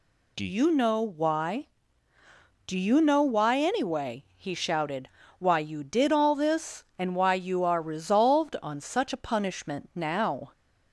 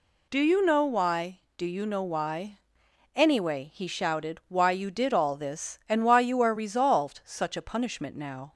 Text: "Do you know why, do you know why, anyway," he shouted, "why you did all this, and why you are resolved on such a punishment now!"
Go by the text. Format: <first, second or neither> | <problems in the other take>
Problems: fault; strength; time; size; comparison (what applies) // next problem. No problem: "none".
first | skips "on"; at 7.2 s